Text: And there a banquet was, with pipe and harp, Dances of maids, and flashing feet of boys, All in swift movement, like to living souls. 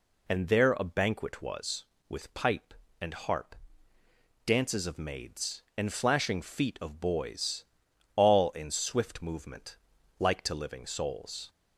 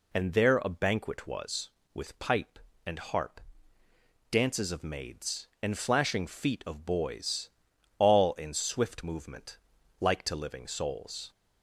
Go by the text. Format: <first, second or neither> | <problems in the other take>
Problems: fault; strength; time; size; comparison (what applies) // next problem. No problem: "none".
neither | none